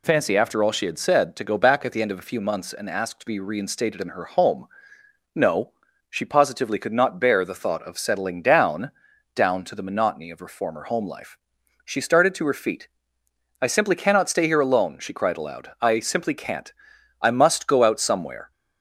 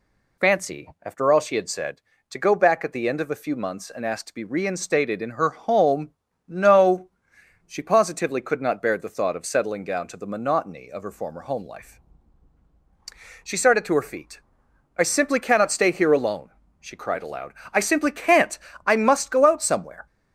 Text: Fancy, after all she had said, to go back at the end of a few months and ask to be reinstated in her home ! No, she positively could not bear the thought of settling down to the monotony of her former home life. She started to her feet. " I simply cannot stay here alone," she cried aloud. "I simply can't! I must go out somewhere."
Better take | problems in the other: second | says "down" twice; at 9.3 s

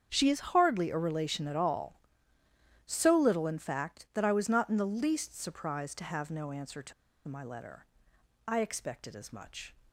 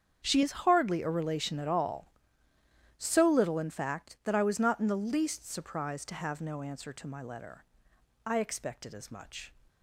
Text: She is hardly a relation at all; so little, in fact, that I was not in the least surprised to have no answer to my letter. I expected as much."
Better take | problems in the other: second | starts louder than the rest; strong; until 1.1 s; 7.5 dB; strong in the second // pauses between "to" and "my"; slight; at 6.9 s; 0.35 s long

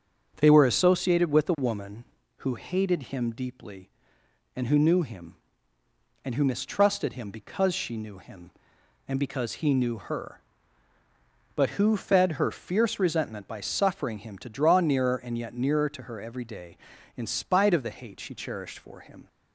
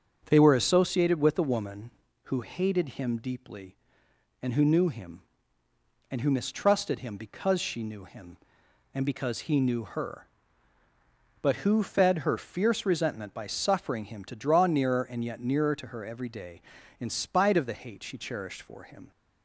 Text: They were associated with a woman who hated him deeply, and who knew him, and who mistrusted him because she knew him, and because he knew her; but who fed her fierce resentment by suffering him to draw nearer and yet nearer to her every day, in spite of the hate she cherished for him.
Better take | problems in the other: neither | starts louder than the rest; the same in both

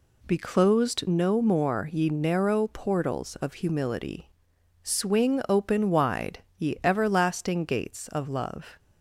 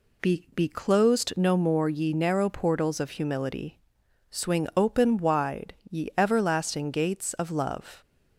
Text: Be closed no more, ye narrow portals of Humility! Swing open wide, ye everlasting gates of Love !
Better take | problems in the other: first | says "Be" twice; at 0.5 s

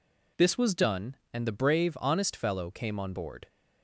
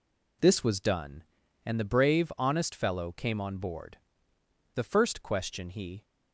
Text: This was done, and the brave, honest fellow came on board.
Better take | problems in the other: first | goes on to say "The first question he"; noticeable; from 4.7 s on; 1.3 s long

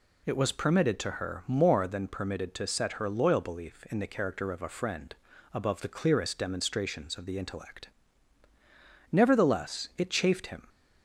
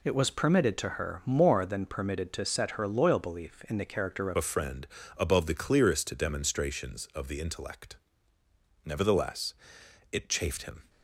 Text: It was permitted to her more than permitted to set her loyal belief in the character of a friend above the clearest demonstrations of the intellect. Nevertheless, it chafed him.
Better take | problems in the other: first | changes voice at "a"; from 4.3 s on; 6.5 s long // pauses between "friend" and "above"; slight; at 4.8 s; 0.30 s long; also in the first

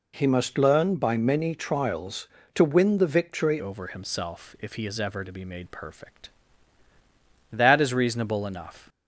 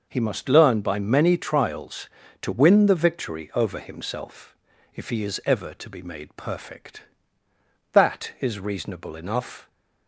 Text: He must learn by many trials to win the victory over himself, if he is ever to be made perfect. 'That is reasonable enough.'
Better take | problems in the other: second | changes voice at "over"; from 3.5 s on; 5.3 s long

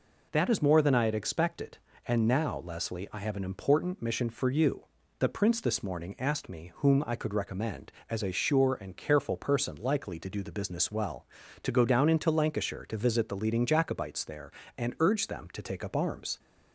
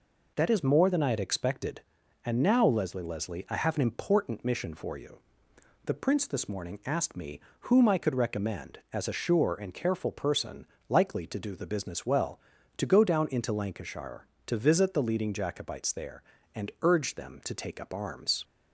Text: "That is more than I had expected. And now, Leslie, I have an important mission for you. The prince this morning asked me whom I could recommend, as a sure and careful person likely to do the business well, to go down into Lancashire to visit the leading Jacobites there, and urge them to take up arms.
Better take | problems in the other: first | says "Leslie" twice; at 3.0 s // pauses between "me" and "whom"; slight; at 7.3 s; 0.28 s long // pauses between "person" and "likely"; slight; at 10.6 s; 0.24 s long

